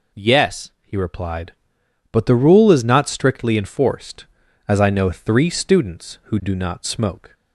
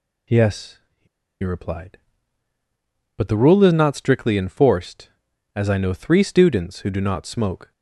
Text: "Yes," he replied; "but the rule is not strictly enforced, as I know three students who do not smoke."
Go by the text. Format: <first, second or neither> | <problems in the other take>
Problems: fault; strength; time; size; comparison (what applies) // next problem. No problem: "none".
first | pauses between "he" and "replied"; at 1.0 s; 0.36 s long